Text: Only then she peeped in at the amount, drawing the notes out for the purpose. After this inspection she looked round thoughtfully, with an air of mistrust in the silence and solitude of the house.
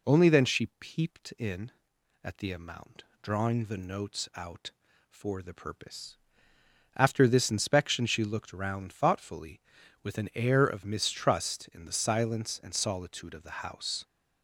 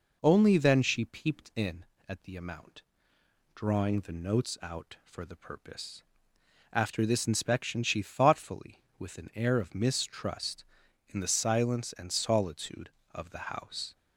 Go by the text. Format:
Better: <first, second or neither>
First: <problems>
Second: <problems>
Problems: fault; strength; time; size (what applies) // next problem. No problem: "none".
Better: first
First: none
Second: skips "looked round"; at 8.0 s